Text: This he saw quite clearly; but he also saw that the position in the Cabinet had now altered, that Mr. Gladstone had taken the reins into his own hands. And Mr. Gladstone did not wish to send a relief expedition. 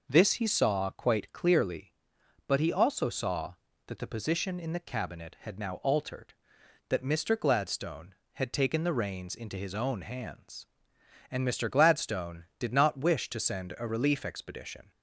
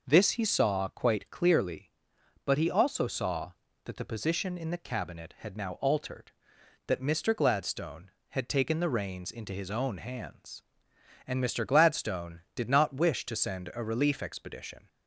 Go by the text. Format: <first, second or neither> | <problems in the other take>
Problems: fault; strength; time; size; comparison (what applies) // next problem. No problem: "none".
neither | none